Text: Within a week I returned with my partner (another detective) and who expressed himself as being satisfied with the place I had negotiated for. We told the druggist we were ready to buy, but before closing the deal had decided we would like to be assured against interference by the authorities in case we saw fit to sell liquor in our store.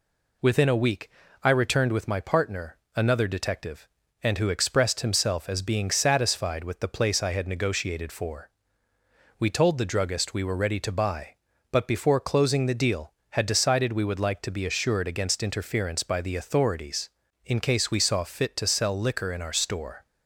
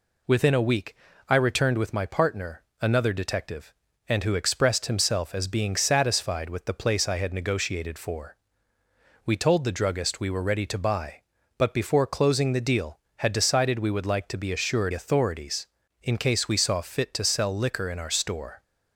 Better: first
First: pauses between "week" and "I"; slight; at 1.1 s; 0.32 s long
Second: pauses between "week" and "I"; slight; at 0.9 s; 0.32 s long // skips "against interference by the"; at 14.9 s

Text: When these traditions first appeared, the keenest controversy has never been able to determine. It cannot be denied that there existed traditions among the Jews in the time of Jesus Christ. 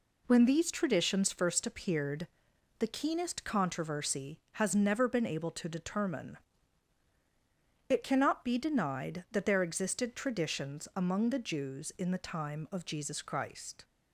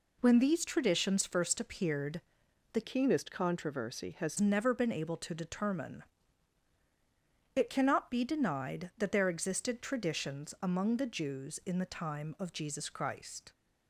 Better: first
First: none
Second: changes voice from "keenest" to "has"; from 2.8 to 4.3 s; 1.5 s long

